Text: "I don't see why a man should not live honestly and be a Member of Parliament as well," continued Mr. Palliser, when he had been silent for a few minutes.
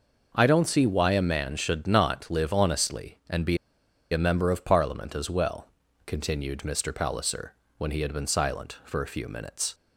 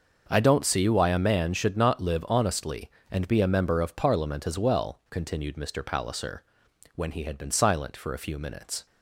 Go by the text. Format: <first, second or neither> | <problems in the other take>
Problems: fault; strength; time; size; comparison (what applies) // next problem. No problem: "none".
second | pauses between "be" and "a"; noticeable; at 3.5 s; 0.54 s long